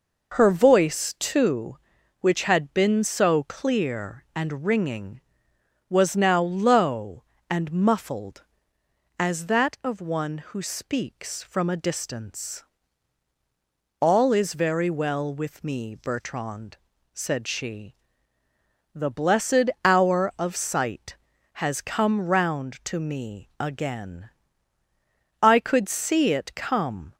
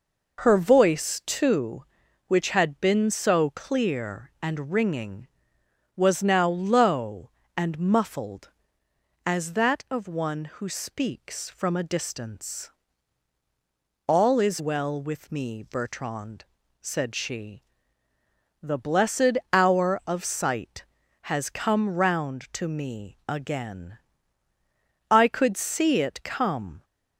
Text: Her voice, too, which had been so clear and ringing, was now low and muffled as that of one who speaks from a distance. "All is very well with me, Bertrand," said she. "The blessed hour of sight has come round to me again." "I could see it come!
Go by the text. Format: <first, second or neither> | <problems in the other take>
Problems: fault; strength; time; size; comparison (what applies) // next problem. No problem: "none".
first | skips "very"; at 14.5 s // pauses between "blessed" and "hour"; slight; at 19.3 s; 0.16 s long; slight in the first